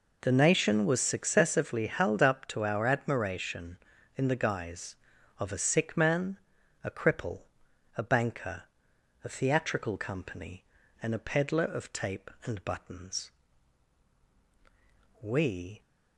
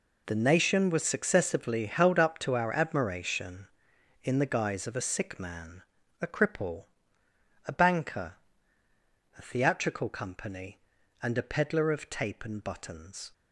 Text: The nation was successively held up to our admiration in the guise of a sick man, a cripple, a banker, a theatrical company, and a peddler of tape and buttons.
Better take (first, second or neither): second